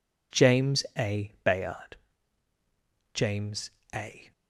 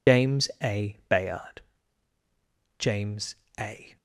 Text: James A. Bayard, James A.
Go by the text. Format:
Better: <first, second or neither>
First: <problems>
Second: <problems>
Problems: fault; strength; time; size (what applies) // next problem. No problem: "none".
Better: first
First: pauses between "James" and "A"; slight; at 3.6 s; 0.24 s long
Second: loses the start of "James"; at 0.0 s; 105 ms // pauses between "James" and "A"; slight; at 3.3 s; 0.24 s long